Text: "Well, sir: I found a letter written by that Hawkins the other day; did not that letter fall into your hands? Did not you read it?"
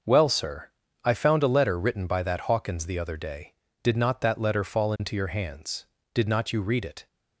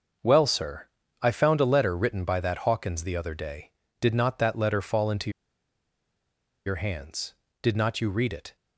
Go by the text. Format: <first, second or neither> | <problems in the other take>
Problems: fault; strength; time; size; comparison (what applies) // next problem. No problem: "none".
first | starts louder than the rest; until 1.5 s; 6.5 dB; also in the first // pauses between "into" and "your"; strong; at 5.3 s; 1.3 s long